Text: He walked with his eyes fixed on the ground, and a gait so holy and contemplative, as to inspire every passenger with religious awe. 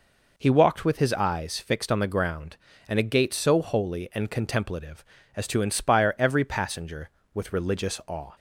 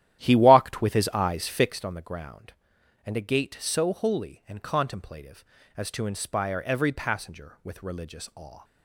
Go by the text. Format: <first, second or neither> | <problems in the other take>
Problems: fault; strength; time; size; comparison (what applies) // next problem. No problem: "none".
first | starts louder than the rest; strong; until 1.9 s; 12 dB